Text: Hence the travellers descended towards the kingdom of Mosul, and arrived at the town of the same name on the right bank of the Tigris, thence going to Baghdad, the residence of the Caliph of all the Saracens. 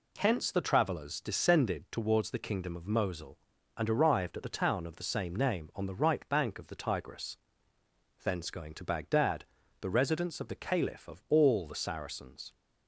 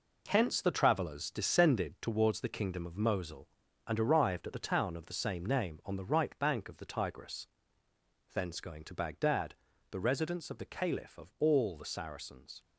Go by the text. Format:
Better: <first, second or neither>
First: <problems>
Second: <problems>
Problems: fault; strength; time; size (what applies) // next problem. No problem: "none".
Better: first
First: none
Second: gets quieter; strong; throughout; 7.5 dB